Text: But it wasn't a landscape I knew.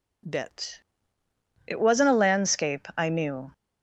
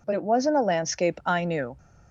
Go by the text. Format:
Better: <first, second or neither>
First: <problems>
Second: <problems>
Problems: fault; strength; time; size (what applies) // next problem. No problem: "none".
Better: second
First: says "Bit" for "But"; at 0.2 s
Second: none